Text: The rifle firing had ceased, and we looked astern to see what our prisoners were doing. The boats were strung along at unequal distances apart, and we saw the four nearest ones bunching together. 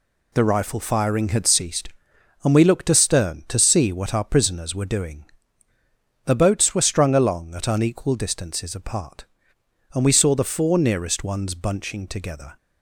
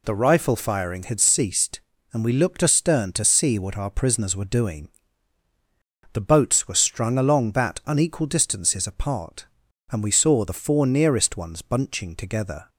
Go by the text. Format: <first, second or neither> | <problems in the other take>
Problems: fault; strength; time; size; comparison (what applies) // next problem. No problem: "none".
first | says "that" for "at"; at 7.5 s